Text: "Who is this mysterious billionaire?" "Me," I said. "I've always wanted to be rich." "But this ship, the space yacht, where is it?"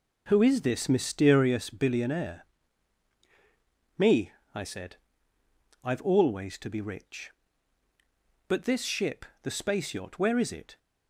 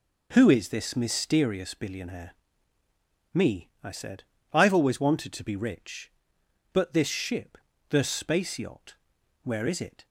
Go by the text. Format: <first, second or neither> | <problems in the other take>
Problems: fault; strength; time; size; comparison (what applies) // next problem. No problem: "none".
second | skips "wanted"; at 6.5 s